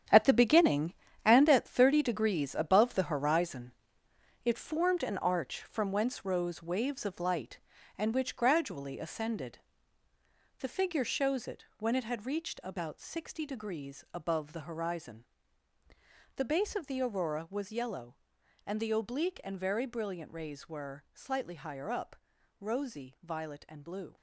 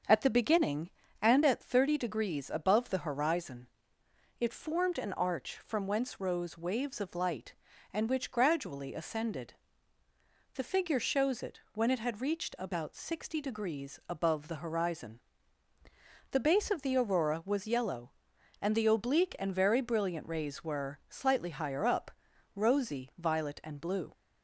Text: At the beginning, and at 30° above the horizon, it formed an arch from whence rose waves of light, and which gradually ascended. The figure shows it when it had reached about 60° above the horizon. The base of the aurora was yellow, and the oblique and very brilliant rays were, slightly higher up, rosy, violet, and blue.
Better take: second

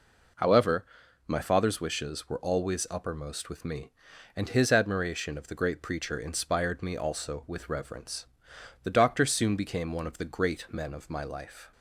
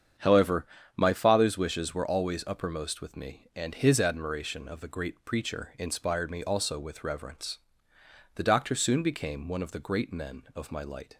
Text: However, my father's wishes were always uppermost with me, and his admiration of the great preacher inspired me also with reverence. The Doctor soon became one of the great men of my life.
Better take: first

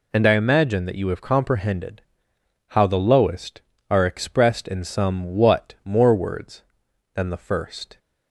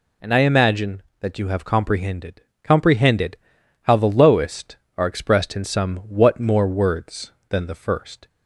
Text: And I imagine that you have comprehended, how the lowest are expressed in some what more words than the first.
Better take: first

